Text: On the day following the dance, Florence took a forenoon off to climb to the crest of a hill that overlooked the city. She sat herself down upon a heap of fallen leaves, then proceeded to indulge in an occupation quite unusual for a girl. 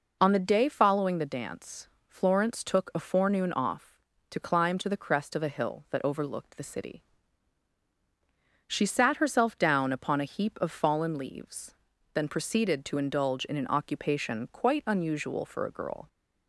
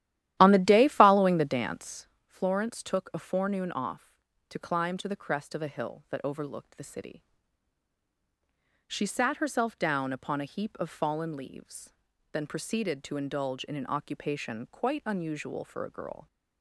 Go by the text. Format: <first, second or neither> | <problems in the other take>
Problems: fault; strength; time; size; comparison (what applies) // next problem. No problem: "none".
first | starts louder than the rest; strong; until 2.1 s; 13 dB